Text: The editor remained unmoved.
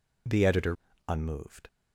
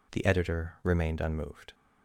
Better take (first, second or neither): second